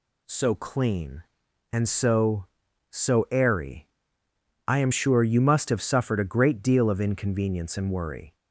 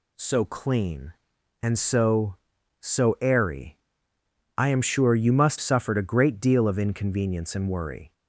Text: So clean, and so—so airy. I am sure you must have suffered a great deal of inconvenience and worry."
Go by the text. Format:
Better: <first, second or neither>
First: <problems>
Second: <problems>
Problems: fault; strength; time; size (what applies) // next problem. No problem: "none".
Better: first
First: none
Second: skips "have"; at 5.5 s